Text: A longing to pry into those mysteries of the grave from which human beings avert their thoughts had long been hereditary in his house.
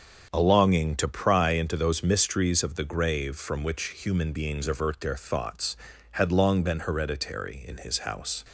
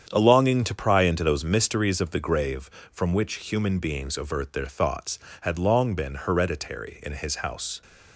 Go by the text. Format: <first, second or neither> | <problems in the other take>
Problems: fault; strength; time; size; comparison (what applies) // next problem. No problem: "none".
neither | starts louder than the rest; strong; the same in both